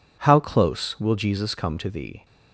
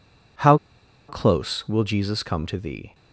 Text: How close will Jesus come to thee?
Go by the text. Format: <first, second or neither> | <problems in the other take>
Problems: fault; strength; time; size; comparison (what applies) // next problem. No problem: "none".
first | pauses between "How" and "close"; noticeable; at 0.5 s; 0.51 s long